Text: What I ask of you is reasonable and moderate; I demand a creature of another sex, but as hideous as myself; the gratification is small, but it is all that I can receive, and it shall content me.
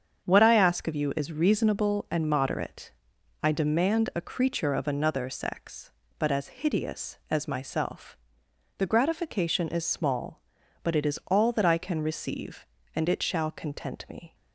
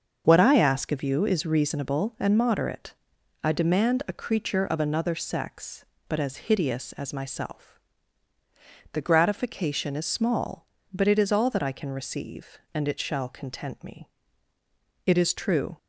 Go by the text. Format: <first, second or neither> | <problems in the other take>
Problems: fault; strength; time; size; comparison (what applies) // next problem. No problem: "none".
first | starts louder than the rest; until 1.2 s; 6.5 dB; strong in the first // goes on to say "It is true"; noticeable; from 15.0 s on; 0.72 s long